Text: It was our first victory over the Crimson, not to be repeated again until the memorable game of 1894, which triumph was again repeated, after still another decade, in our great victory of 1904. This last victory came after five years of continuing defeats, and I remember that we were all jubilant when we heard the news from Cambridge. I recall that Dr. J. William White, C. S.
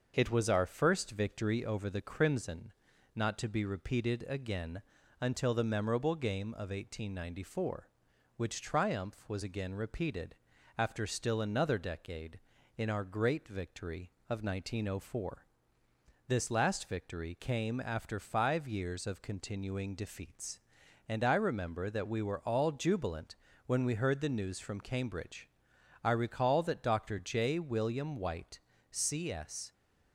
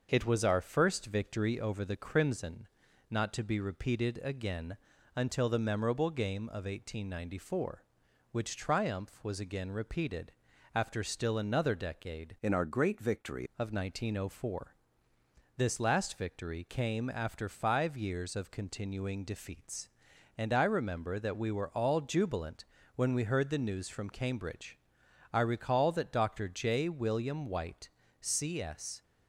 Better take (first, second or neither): first